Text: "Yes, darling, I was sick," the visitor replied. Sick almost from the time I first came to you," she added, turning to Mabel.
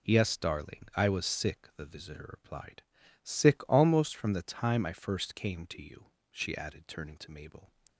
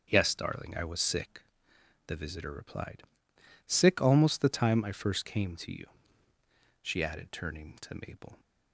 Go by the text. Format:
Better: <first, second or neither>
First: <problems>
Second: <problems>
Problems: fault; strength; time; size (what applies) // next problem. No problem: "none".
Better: first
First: none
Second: starts louder than the rest; until 1.1 s; 6.5 dB // skips "from"; at 4.3 s